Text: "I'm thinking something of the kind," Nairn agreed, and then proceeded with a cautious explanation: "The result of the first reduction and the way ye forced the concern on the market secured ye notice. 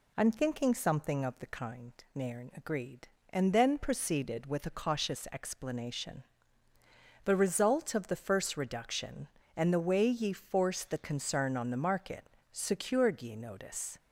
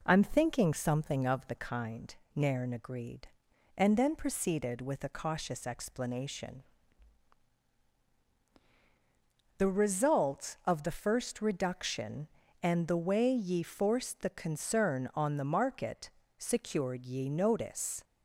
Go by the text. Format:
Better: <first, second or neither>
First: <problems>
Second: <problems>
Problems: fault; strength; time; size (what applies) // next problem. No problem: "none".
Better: neither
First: pauses between "market" and "secured"; slight; at 12.2 s; 0.22 s long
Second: pauses between "market" and "secured"; slight; at 16.0 s; 0.26 s long